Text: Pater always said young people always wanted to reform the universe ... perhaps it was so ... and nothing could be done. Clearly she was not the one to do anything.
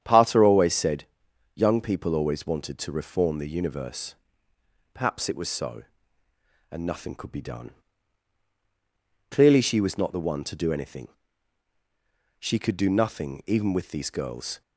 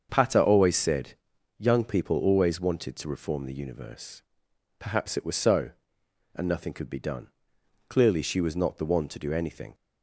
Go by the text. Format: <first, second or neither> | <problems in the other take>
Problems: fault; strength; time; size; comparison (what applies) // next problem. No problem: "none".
second | starts louder than the rest; strong; until 1.0 s; 8.5 dB; also in the second // pauses between "said" and "young"; noticeable; at 1.0 s; 0.52 s long; also in the second // goes on to say "She could do nothing even with these girls"; strong; from 12.3 s on; 2.2 s long